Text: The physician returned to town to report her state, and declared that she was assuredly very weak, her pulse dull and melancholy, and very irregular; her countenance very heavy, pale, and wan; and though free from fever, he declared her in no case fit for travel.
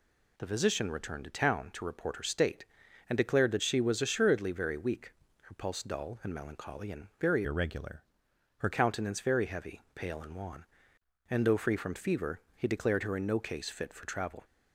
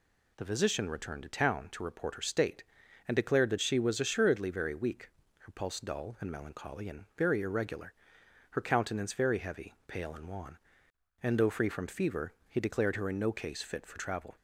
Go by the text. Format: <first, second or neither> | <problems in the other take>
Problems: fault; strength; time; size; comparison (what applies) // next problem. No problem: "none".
second | changes voice from "irregular" to "her"; from 7.4 to 8.6 s; 1.2 s long